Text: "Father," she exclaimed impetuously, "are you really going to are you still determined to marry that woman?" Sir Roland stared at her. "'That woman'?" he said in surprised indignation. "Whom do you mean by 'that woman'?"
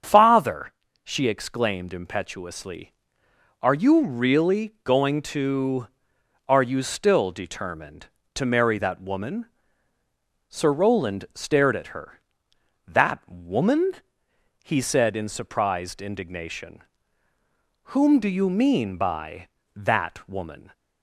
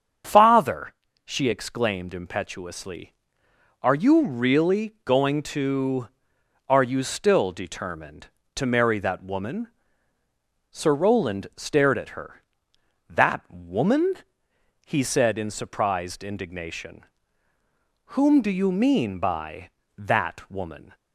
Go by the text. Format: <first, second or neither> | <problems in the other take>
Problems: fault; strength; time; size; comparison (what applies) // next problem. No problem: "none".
neither | starts louder than the rest; strong; the same in both